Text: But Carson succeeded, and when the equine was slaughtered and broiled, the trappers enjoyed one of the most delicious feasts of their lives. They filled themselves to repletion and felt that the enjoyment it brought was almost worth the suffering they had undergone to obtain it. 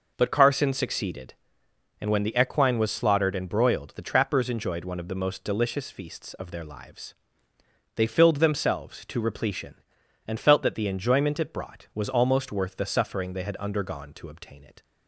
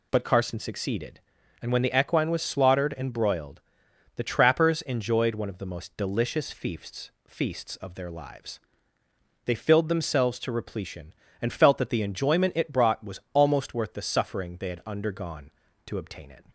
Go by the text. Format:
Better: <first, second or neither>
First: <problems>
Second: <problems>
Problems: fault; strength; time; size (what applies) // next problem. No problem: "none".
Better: first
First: none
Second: says "feasts" twice; at 7.2 s